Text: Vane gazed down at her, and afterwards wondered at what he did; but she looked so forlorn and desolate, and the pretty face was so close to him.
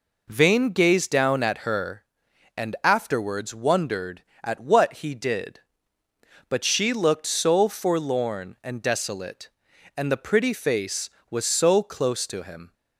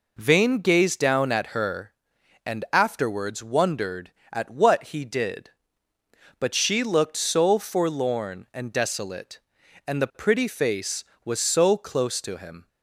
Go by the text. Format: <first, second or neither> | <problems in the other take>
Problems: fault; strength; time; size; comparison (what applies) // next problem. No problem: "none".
neither | none